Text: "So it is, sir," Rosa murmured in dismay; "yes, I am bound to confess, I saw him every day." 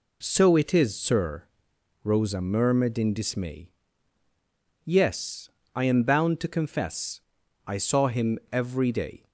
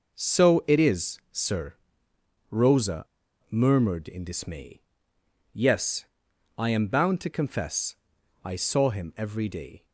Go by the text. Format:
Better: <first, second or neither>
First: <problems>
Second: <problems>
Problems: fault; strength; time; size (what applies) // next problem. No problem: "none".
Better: first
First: none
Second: pauses between "Rosa" and "murmured"; at 3.0 s; 0.43 s long